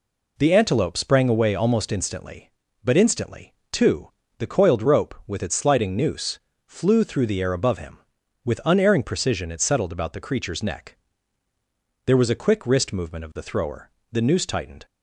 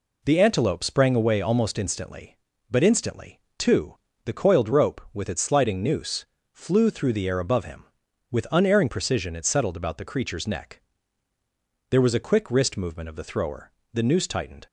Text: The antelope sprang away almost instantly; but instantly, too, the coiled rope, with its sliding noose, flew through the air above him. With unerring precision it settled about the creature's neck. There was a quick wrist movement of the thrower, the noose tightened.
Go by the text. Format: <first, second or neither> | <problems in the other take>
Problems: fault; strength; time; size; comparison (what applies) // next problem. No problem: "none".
neither | none